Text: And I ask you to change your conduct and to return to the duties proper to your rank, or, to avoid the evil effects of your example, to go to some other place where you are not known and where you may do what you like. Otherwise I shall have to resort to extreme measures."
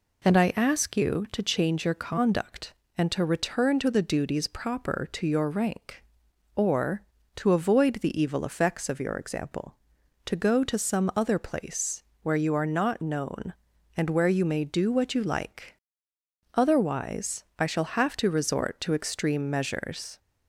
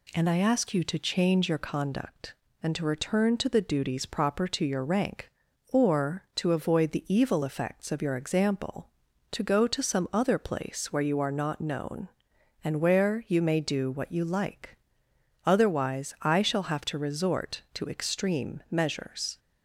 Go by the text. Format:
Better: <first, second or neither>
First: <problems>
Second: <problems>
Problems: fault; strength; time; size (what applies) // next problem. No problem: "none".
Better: second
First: starts louder than the rest; slight; until 1.2 s; 3.5 dB // pauses between "place" and "where"; slight; at 12.0 s; 0.20 s long // pauses between "Otherwise" and "I"; slight; at 17.4 s; 0.16 s long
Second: none